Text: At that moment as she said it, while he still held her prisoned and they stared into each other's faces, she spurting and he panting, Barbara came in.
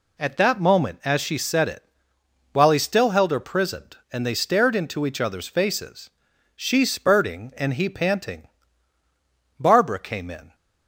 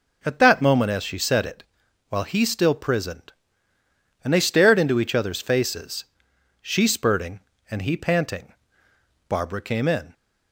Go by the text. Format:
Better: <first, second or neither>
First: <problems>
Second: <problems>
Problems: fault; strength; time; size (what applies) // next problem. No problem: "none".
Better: first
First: none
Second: skips "held her"; at 2.7 s